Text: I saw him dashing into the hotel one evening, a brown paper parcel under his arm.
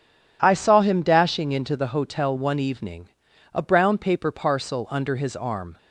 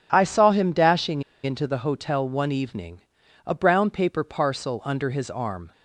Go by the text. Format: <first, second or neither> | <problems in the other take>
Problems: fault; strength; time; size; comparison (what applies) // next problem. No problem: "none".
first | pauses between "dashing" and "into"; slight; at 1.2 s; 0.22 s long